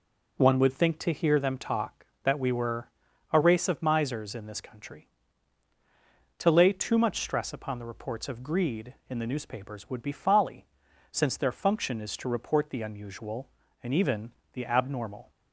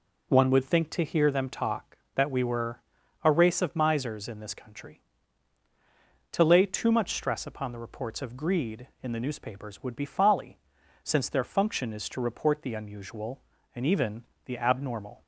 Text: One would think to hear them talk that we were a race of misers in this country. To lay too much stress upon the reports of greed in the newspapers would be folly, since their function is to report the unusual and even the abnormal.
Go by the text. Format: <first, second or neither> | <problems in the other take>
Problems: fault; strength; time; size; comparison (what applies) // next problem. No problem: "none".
neither | pauses between "were" and "a"; the same in both // pauses between "even" and "the"; slight; the same in both